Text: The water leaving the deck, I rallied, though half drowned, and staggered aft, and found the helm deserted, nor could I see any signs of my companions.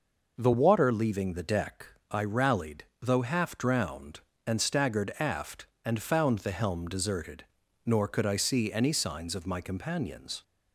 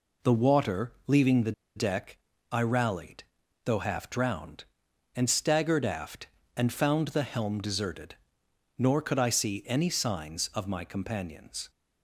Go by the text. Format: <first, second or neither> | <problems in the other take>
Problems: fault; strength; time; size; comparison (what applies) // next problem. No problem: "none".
first | pauses between "the" and "deck"; slight; at 1.5 s; 0.23 s long